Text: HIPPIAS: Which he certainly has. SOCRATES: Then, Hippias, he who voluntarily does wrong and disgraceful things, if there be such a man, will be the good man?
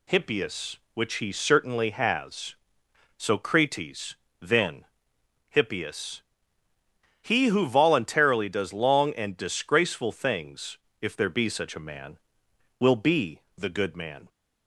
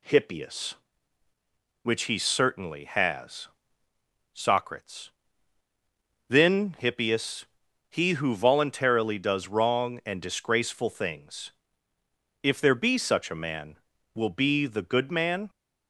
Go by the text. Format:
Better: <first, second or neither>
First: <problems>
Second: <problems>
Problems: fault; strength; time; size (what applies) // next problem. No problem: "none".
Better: second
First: says "long" for "wrong"; at 8.7 s // pauses between "be" and "the"; slight; at 13.4 s; 0.16 s long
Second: none